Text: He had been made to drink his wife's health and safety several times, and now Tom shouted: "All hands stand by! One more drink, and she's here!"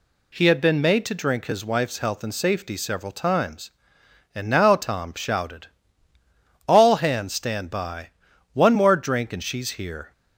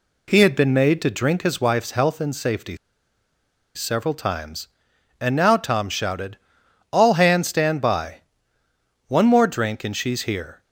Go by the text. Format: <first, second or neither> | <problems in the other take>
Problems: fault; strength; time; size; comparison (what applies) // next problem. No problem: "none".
first | pauses between "safety" and "several"; at 2.7 s; 0.98 s long